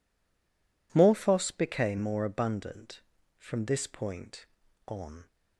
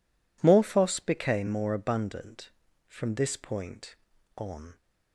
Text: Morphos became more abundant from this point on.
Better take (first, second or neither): second